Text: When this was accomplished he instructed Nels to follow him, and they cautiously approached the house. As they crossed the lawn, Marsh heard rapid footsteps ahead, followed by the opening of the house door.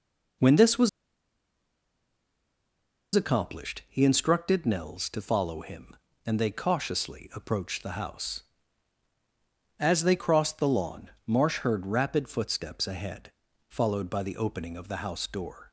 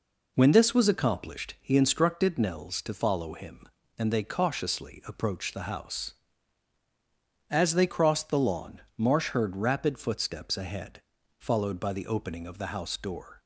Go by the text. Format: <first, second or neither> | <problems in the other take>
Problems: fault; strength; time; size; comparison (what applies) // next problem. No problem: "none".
second | pauses between "was" and "accomplished"; strong; at 0.8 s; 2.2 s long